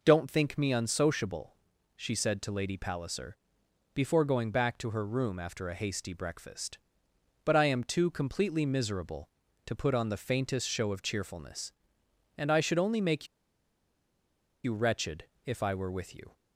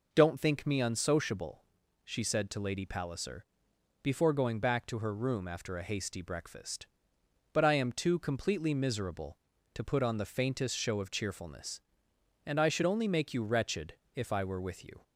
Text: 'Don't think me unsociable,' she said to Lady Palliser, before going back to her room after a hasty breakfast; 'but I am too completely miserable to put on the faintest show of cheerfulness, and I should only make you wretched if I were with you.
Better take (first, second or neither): second